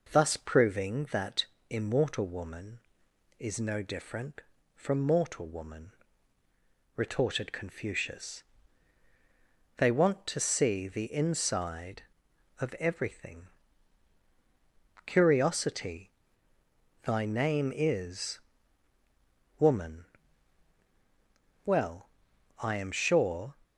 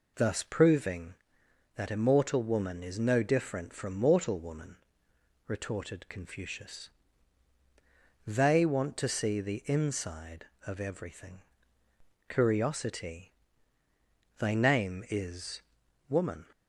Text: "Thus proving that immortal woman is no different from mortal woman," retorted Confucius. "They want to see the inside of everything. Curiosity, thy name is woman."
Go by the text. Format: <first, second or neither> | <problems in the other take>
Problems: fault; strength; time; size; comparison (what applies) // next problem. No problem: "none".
second | pauses between "that" and "immortal"; slight; at 1.4 s; 0.24 s long // pauses between "is" and "woman"; at 18.3 s; 1.2 s long; noticeable in the second // goes on to say "Well I am sure"; strong; from 21.6 s on; 1.8 s long